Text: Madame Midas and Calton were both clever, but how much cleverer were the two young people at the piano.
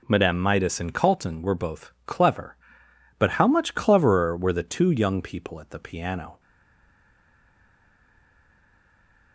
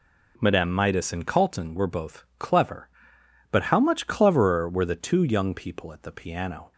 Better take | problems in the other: second | stays silent after the last word; strong; from 6.3 s on; 3.0 s long

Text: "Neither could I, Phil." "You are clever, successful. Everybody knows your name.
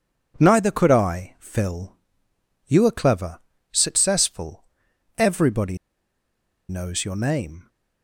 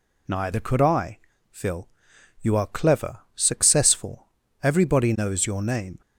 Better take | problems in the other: second | pauses between "Everybody" and "knows"; noticeable; at 5.7 s; 0.91 s long

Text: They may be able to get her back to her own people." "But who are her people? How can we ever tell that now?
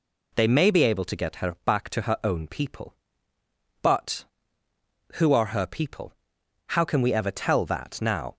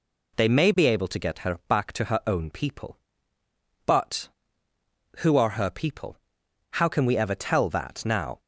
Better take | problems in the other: neither | none

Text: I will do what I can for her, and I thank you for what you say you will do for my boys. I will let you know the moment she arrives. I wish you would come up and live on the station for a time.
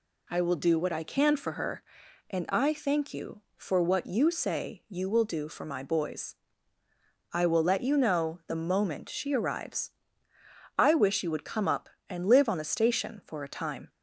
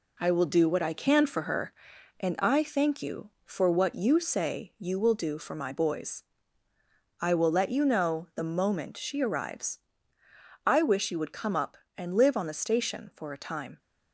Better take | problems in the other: first | gets quieter; noticeable; throughout; 4 dB

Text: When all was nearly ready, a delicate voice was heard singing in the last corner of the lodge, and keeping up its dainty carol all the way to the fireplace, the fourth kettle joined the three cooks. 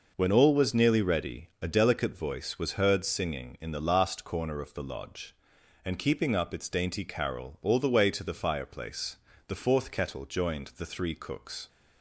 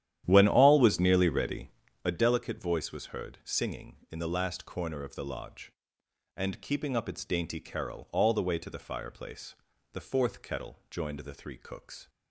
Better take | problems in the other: first | starts louder than the rest; strong; until 2.1 s; 11 dB

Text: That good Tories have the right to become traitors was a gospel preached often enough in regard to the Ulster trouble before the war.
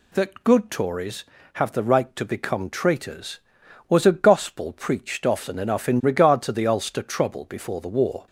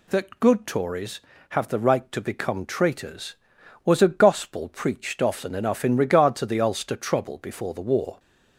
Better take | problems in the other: neither | none

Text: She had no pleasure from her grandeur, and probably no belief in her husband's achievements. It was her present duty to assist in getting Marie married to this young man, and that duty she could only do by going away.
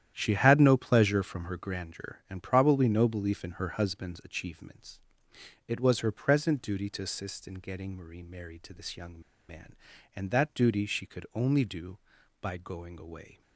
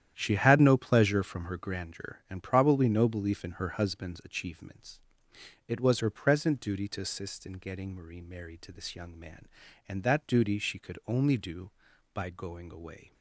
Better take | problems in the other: second | starts louder than the rest; strong; until 1.1 s; 10.5 dB; strong in the second // pauses between "young" and "man"; slight; at 9.2 s; 0.28 s long

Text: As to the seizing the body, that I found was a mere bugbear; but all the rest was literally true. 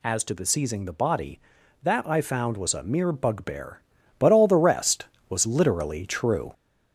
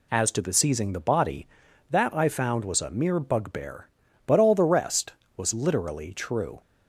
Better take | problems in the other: second | gets louder; slight; throughout; 3 dB

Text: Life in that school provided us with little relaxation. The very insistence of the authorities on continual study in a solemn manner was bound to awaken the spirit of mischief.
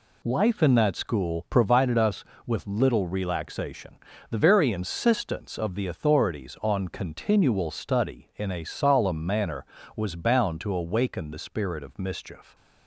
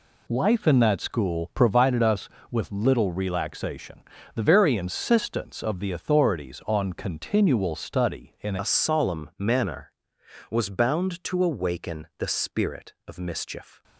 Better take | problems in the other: first | changes voice at "a"; from 8.5 s on; 5.3 s long

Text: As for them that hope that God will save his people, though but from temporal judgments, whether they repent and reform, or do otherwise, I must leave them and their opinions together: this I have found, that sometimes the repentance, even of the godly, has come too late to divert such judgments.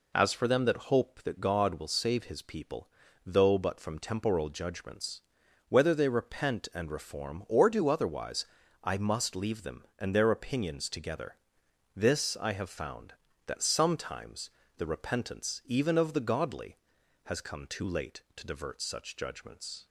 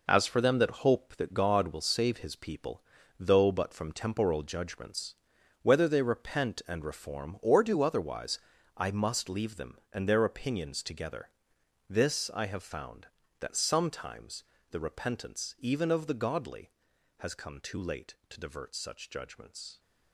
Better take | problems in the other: first | gets quieter; strong; throughout; 8 dB // pauses between "sometimes" and "the"; slight; at 14.4 s; 0.28 s long; slight in the first

